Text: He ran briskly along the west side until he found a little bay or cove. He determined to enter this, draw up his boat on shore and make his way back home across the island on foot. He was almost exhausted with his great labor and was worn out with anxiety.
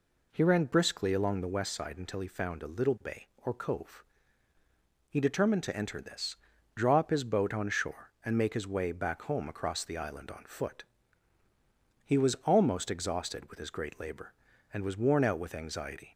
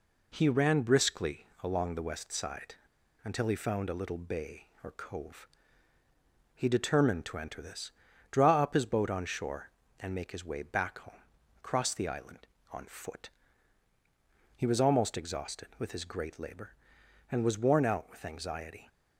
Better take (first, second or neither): first